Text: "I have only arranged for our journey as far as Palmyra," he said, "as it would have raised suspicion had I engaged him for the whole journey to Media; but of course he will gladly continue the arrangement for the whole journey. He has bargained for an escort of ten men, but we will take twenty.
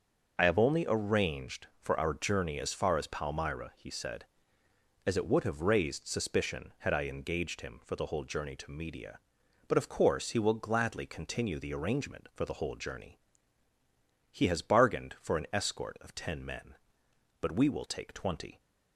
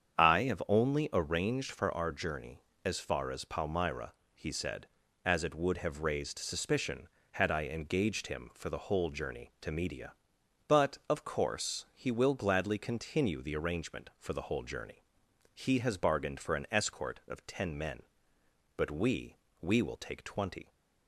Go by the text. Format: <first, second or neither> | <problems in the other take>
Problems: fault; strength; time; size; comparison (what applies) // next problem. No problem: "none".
first | starts louder than the rest; strong; until 1.2 s; 8 dB; also in the first // says "we" twice; at 19.6 s